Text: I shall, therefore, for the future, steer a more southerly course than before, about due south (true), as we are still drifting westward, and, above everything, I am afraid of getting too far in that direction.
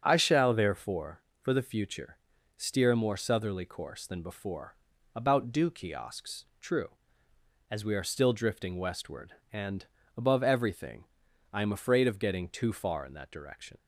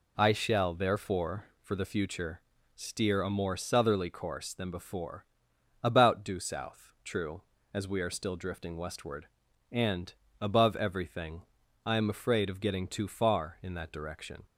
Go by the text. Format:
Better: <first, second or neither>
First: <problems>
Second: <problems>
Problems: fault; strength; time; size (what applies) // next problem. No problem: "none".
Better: second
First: starts louder than the rest; until 1.0 s; 7 dB // says "kiosks" for "south"; at 5.6 s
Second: none